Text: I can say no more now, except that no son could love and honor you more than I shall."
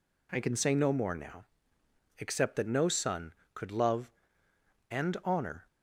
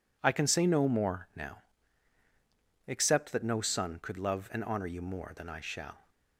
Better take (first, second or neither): second